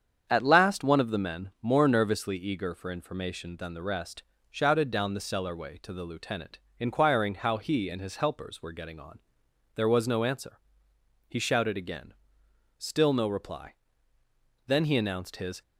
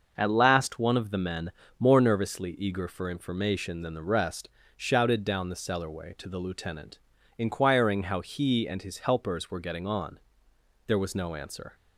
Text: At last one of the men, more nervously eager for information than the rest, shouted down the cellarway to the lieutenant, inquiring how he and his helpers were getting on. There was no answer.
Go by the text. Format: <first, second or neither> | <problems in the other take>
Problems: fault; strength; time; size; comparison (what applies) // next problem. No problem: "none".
second | starts louder than the rest; strong; until 1.3 s; 8 dB // goes on to say "He shouted again Still no reply Then he announced his"; strong; from 11.2 s on; 4.3 s long